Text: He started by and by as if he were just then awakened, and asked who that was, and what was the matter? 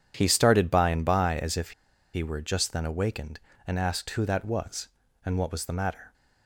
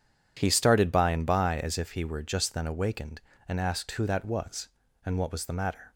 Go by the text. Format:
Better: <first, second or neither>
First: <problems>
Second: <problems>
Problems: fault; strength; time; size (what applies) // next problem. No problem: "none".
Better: second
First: pauses between "if" and "he"; at 1.7 s; 0.42 s long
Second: none